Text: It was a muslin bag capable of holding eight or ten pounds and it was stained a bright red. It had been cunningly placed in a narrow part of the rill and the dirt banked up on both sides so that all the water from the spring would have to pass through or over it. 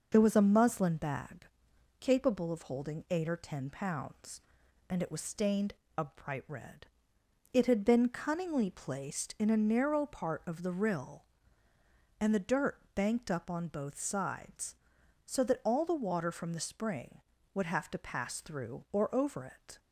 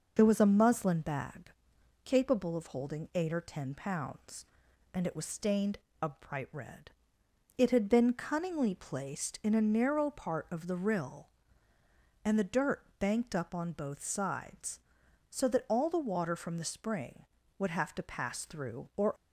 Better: first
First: pauses between "bag" and "capable"; noticeable; at 1.4 s; 0.52 s long // pauses between "stained" and "a"; slight; at 5.7 s; 0.24 s long // pauses between "dirt" and "banked"; slight; at 12.7 s; 0.16 s long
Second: pauses between "bag" and "capable"; noticeable; at 1.5 s; 0.52 s long // pauses between "stained" and "a"; slight; at 5.7 s; 0.24 s long // pauses between "dirt" and "banked"; slight; at 12.8 s; 0.16 s long // stops before "over it"; at 19.1 s

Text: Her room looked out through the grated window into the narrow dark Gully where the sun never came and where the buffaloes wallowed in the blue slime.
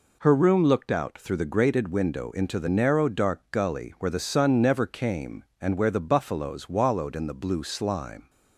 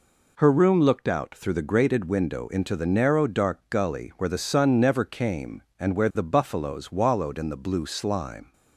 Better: neither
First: none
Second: none

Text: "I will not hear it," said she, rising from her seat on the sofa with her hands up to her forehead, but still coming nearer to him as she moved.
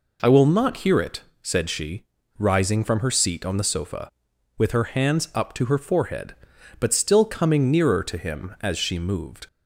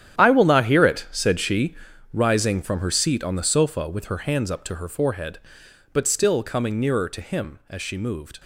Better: first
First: none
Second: gets quieter; strong; throughout; 14 dB

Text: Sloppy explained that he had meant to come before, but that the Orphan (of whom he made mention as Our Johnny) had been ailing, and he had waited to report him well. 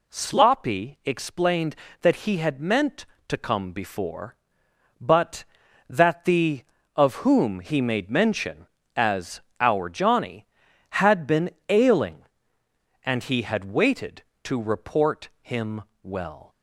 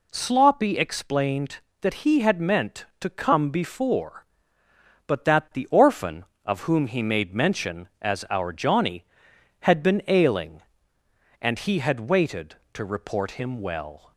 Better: second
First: skips "Orphan"; at 6.7 s // pauses between "as" and "Our"; slight; at 9.3 s; 0.20 s long // pauses between "been" and "ailing"; slight; at 11.4 s; 0.18 s long // pauses between "him" and "well"; slight; at 15.8 s; 0.22 s long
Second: none

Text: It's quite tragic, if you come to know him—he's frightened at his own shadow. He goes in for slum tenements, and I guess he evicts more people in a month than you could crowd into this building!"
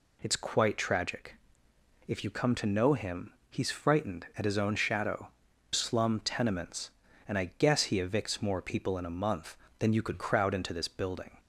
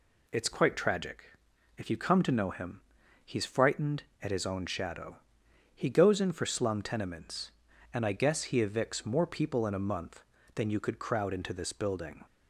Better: second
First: skips "He goes in for"; at 5.5 s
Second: none

